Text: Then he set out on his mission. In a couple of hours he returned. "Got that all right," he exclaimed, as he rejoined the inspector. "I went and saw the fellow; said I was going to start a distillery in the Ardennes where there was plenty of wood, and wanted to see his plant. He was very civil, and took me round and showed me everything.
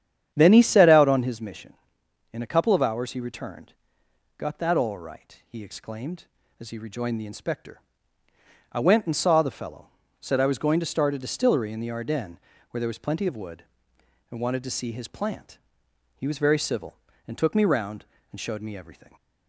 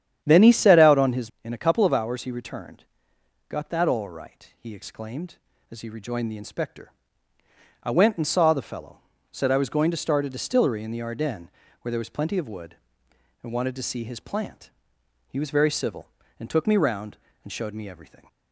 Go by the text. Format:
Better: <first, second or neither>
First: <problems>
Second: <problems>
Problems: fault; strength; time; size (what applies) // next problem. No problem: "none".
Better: first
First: starts louder than the rest; strong; until 1.3 s; 9 dB // pauses between "Ardennes" and "where"; slight; at 12.3 s; 0.32 s long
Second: starts louder than the rest; strong; until 1.2 s; 9.5 dB // skips "mission"; at 1.3 s // pauses between "Ardennes" and "where"; slight; at 11.4 s; 0.32 s long